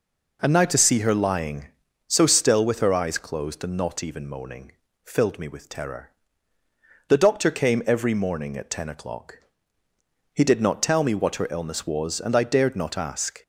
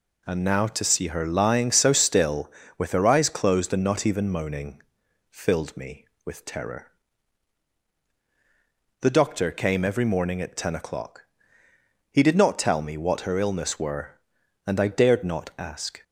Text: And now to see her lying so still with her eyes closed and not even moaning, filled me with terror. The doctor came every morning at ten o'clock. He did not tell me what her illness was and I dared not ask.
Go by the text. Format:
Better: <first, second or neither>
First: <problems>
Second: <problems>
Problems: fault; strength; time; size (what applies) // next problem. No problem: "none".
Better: first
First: none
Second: says "were" for "was"; at 13.7 s